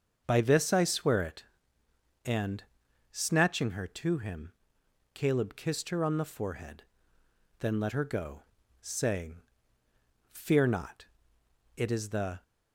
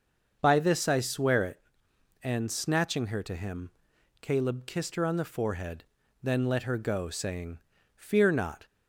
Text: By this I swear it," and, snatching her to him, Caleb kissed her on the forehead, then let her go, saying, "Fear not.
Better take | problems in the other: second | starts louder than the rest; until 1.2 s; 6.5 dB; also in the second // goes on to say "It is the"; noticeable; from 11.7 s on; 0.68 s long

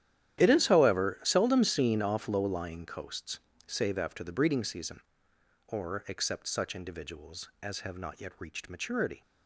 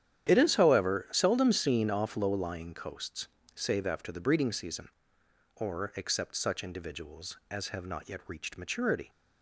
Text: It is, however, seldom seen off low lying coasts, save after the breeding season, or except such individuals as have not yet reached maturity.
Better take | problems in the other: second | gets quieter; strong; throughout; 16 dB // starts louder than the rest; strong; until 1.4 s; 11 dB; strong in the second

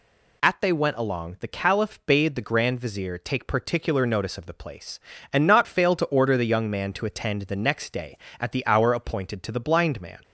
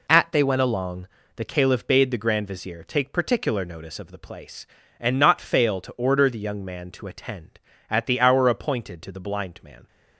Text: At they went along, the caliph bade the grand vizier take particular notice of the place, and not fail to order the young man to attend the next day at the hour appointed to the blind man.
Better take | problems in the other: first | skips "the next day"; at 7.7 s

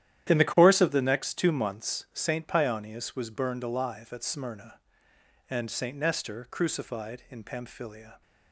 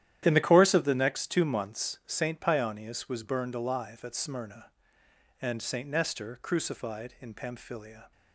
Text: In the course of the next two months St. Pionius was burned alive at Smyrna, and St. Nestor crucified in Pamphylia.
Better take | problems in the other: neither | starts louder than the rest; strong; the same in both

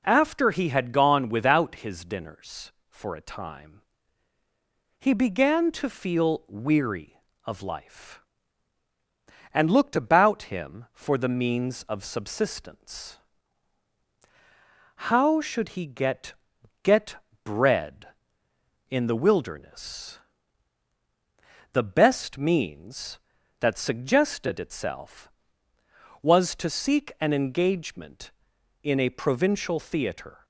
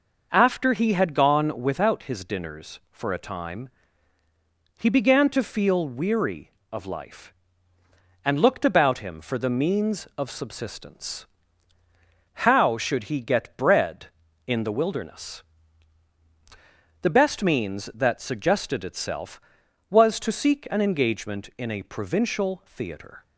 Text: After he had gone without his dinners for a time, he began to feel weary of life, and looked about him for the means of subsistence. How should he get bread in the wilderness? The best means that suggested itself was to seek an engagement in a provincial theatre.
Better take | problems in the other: second | says "get" twice; at 16.8 s

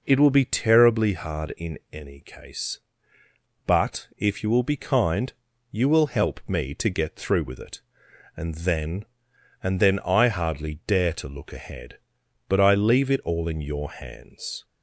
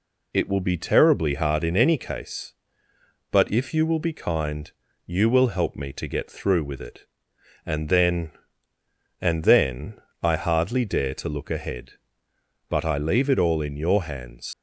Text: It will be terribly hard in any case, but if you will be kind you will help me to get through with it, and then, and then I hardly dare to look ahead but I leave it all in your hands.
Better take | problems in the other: first | pauses between "kind" and "you"; at 4.7 s; 0.38 s long; also in the first // pauses between "then" and "I"; slight; at 9.9 s; 0.24 s long // leaves "hands" unfinished; at 14.5 s; 85 ms

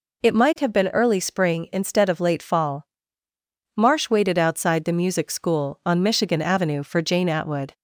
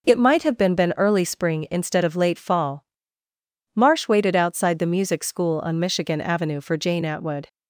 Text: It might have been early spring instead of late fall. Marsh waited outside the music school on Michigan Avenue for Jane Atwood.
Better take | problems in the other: first | says "been" twice; at 0.7 s

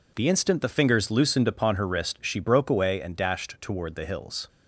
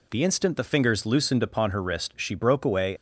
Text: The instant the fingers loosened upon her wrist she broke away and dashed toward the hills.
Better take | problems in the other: first | stops before "and dashed toward the hills"; at 2.9 s

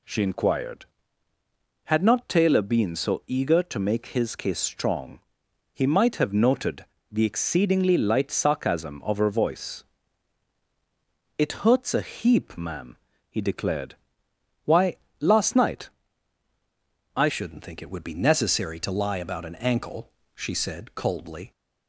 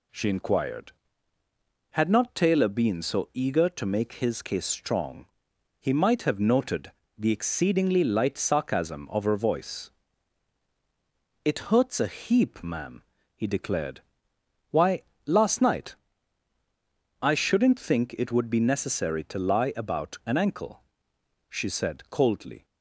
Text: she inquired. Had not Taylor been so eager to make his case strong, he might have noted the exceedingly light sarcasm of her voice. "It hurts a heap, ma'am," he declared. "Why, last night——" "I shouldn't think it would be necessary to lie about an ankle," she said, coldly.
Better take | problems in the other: second | pauses between "noted" and "the"; slight; at 6.8 s; 0.26 s long; slight in the second // changes voice at "shouldn't"; from 17.2 s on; 4.3 s long

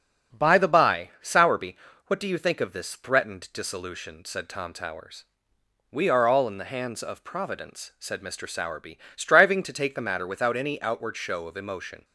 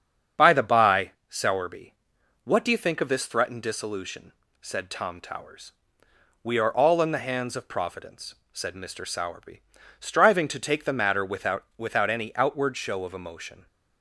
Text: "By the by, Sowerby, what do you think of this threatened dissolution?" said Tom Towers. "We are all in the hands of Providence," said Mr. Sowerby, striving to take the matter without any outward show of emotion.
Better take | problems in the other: first | starts louder than the rest; strong; until 1.5 s; 7.5 dB; also in the first // says "without" twice; at 11.7 s

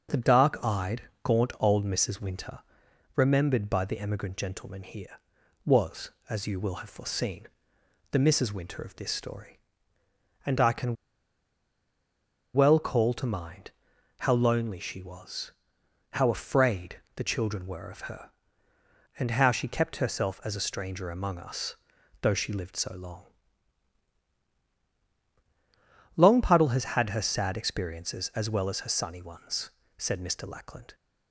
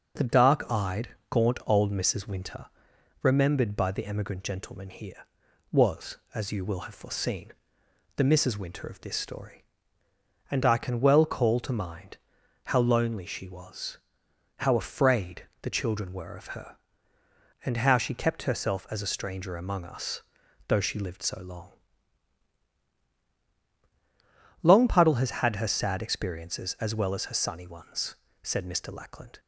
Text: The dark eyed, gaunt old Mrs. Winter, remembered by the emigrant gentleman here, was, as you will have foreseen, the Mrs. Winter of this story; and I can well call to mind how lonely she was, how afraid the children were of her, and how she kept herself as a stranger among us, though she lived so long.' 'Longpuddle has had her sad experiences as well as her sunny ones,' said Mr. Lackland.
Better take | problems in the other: second | starts louder than the rest; until 1.2 s; 6.5 dB; also in the second // pauses between "can" and "well"; strong; at 10.9 s; 1.5 s long // pauses between "mind" and "how"; noticeable; at 13.7 s; 0.50 s long; noticeable in the second

